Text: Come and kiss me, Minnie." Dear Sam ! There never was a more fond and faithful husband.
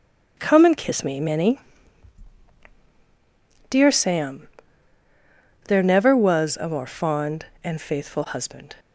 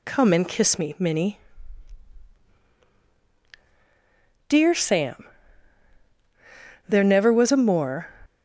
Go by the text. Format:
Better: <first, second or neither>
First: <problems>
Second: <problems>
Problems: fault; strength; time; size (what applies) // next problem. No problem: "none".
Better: first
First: none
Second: stops before "fond and faithful husband"; at 8.2 s